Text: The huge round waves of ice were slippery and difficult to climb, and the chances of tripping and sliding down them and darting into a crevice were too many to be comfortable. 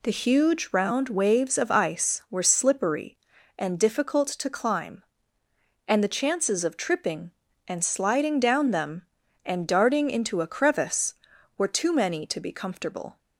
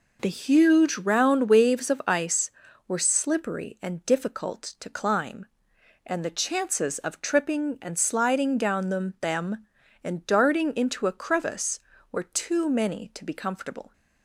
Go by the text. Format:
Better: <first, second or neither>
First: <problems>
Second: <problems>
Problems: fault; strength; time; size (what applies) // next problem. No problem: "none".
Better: first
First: none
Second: says "them" twice; at 9.2 s